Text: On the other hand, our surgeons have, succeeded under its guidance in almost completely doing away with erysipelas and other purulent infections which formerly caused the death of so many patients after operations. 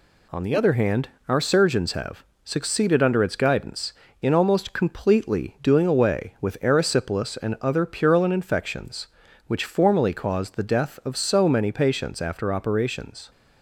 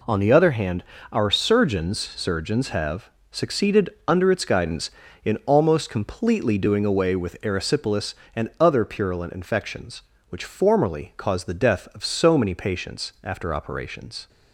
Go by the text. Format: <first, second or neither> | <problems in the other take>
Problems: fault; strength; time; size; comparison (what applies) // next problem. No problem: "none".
first | says "surgeons" twice; at 1.9 s // pauses between "succeeded" and "under"; slight; at 3.8 s; 0.20 s long